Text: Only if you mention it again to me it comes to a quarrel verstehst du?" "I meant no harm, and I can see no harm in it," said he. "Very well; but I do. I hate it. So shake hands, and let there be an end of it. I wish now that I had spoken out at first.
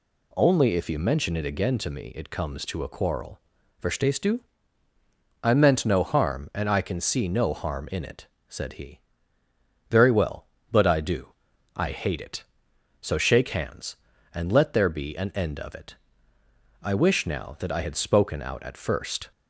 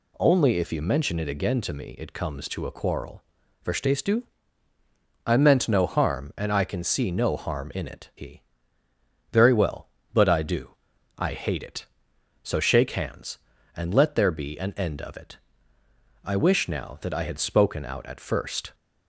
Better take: first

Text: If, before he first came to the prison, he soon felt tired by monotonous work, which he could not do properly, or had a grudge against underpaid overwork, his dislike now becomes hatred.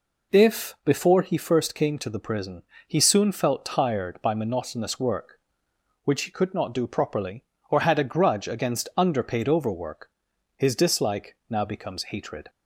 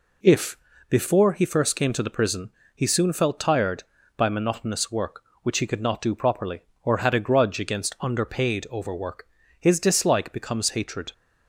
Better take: first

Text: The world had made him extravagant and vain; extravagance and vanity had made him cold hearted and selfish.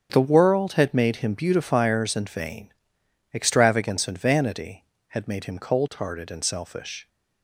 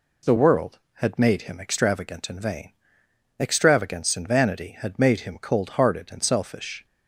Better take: second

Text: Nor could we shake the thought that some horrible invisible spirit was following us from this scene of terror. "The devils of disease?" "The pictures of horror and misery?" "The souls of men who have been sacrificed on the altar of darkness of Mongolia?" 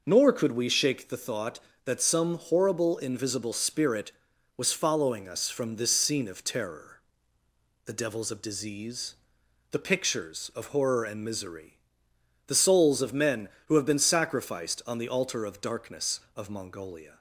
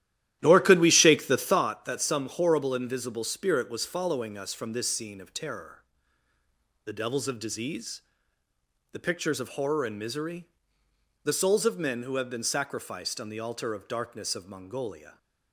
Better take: first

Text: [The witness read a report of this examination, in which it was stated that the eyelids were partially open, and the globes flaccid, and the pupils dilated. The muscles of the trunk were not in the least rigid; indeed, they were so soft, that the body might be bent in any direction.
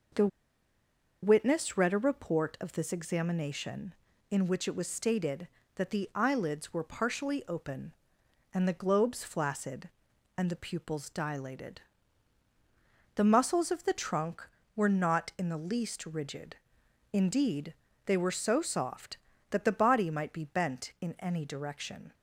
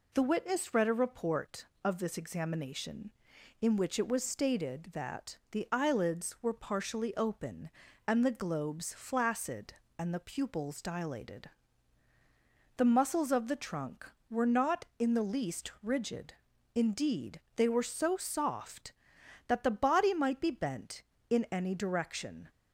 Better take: second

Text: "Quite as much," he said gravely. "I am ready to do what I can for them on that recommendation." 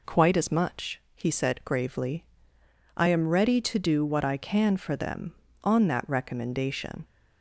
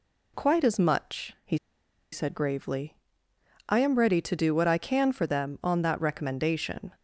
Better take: first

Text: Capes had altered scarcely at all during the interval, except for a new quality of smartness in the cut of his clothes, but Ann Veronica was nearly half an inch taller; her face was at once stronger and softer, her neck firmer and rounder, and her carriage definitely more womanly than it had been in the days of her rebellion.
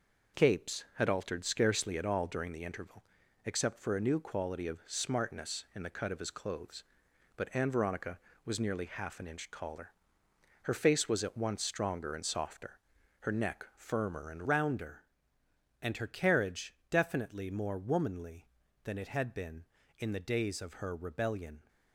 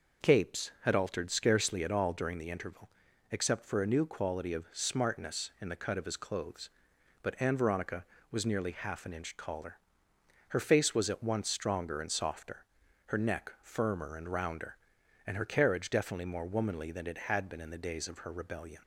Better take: second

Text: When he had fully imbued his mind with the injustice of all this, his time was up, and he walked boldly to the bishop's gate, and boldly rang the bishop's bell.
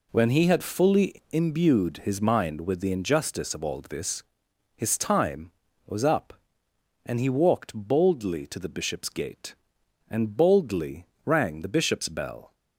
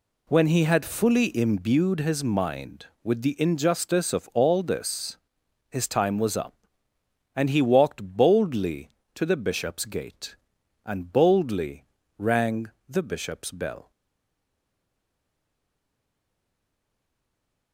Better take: first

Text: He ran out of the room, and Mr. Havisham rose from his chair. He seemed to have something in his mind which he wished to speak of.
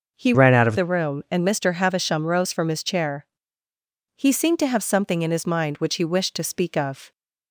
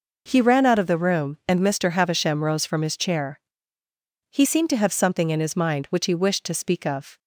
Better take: second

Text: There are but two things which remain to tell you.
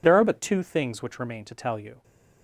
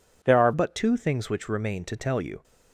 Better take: first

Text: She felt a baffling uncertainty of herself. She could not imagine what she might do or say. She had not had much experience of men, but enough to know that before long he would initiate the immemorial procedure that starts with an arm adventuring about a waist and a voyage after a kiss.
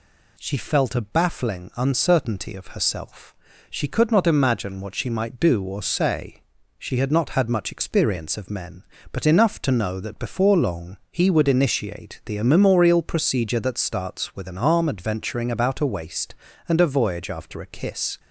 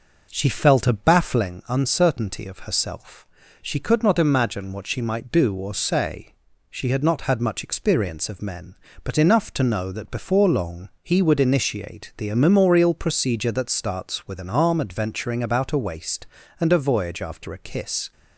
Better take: first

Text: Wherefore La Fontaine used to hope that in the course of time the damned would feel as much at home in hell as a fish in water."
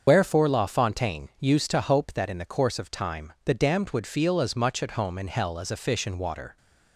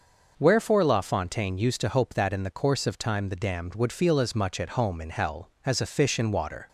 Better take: second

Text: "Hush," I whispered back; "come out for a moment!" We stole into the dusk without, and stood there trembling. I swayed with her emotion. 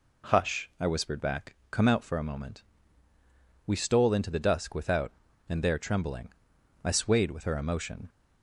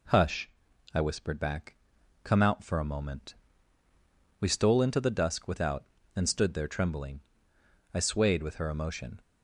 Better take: second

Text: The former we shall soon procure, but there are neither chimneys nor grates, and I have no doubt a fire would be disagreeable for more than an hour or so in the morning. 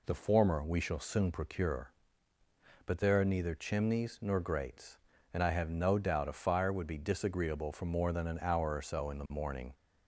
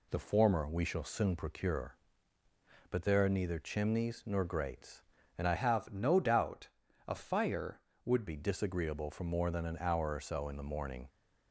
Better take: first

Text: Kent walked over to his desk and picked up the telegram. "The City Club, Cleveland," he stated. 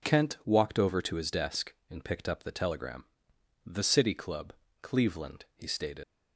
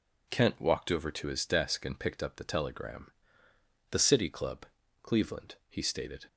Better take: second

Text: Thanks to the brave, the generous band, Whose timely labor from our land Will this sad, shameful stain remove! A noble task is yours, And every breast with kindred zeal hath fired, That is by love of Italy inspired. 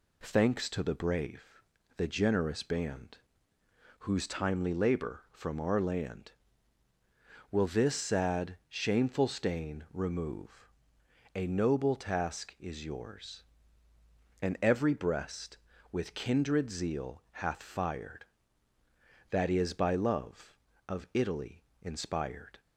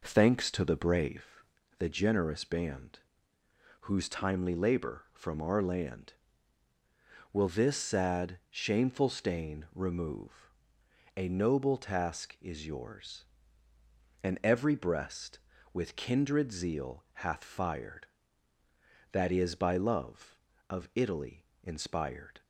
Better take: first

